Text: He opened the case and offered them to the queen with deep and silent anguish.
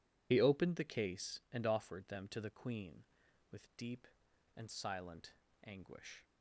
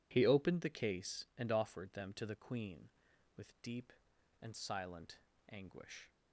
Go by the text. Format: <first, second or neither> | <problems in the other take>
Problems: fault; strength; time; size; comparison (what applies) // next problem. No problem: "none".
second | loses the start of "He"; at 0.3 s; 50 ms // pauses between "silent" and "anguish"; slight; at 5.3 s; 0.34 s long; slight in the second